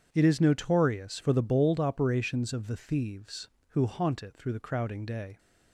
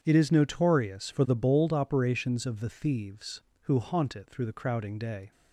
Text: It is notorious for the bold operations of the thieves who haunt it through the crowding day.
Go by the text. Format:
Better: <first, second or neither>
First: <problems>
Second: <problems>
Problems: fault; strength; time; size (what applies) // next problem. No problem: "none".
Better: neither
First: starts louder than the rest; strong; until 1.1 s; 8 dB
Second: starts louder than the rest; strong; until 1.0 s; 8 dB